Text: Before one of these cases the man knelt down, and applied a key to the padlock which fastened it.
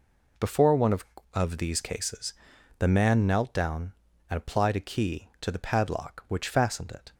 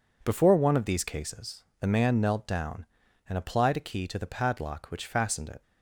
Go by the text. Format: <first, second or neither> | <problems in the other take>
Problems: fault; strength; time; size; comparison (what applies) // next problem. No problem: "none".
second | says "of" twice; at 1.3 s // pauses between "cases" and "the"; noticeable; at 2.3 s; 0.46 s long; slight in the second